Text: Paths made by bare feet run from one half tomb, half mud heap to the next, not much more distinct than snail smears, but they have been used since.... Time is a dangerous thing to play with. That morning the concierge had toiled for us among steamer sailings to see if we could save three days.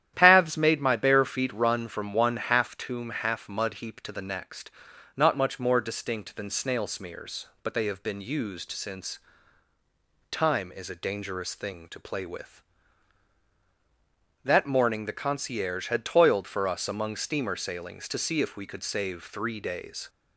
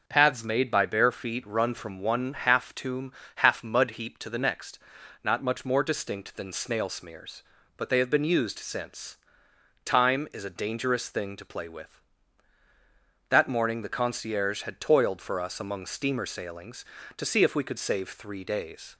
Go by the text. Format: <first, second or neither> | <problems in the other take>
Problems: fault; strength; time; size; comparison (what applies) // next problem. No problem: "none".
second | starts louder than the rest; strong; until 1.1 s; 11 dB; noticeable in the second // says "my" for "by"; at 0.7 s